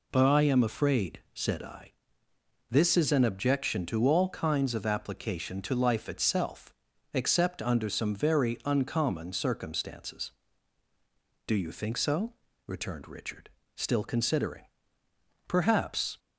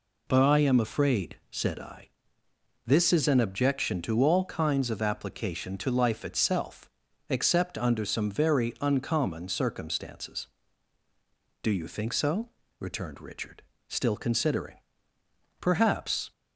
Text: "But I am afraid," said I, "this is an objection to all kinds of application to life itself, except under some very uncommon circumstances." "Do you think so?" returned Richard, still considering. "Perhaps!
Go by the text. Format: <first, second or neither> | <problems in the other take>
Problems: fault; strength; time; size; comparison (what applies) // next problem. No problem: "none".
neither | none